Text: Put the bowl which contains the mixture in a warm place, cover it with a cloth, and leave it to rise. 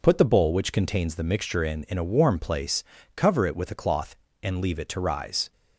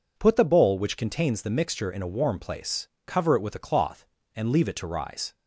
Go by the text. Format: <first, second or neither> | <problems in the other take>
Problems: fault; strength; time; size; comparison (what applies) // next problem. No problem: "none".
second | says "in" twice; at 1.8 s